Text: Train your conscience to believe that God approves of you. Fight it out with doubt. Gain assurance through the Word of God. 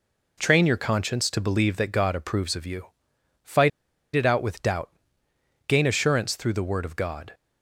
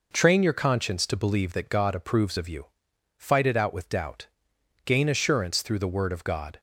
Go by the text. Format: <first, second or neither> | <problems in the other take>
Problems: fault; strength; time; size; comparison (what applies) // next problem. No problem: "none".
second | pauses between "Fight" and "it"; at 3.6 s; 0.45 s long